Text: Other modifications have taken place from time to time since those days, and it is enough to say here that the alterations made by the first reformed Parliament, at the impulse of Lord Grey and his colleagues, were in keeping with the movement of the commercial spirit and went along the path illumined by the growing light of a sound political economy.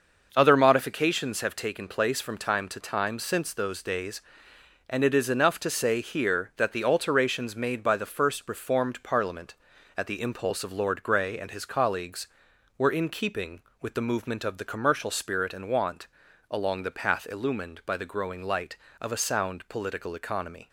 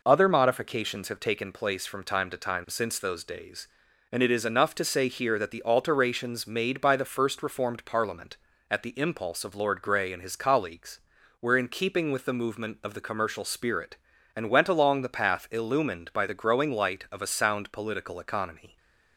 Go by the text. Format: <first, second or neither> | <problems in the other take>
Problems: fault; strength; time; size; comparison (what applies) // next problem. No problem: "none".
second | starts louder than the rest; noticeable; until 1.3 s; 6 dB // says "want" for "went"; at 15.7 s